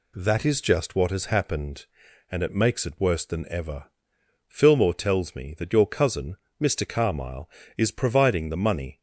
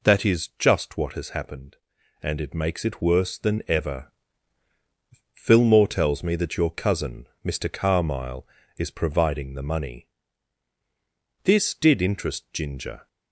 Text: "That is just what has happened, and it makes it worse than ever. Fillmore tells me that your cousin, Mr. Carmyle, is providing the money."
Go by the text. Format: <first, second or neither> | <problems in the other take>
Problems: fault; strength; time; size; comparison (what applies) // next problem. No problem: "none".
first | goes on to say "This did interest Ginger"; from 11.4 s on; 1.6 s long